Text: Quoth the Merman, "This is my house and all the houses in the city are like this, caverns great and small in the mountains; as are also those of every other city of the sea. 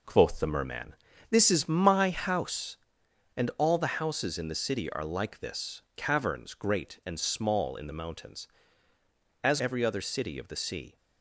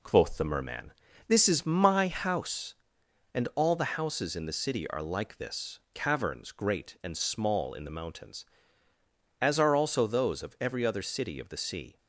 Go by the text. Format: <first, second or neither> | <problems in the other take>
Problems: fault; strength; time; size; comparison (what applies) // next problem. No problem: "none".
second | skips "are also those of"; at 9.5 s